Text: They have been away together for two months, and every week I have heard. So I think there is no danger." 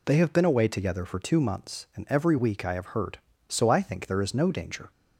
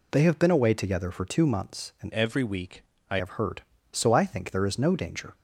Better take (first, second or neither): first